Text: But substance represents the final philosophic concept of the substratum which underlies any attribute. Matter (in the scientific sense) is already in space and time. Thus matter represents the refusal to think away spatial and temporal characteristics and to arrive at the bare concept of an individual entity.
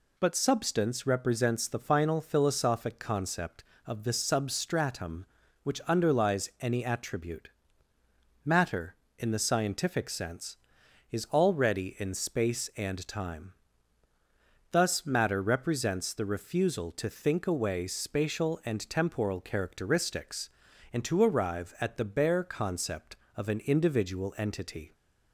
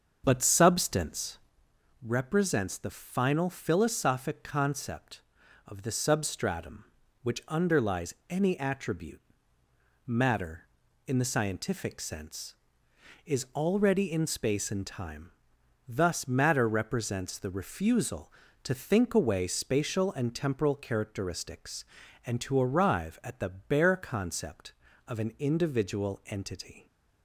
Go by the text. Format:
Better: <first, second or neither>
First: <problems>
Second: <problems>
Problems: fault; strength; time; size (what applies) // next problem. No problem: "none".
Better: first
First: none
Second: starts louder than the rest; until 1.6 s; 7 dB // pauses between "substance" and "represents"; noticeable; at 1.3 s; 0.64 s long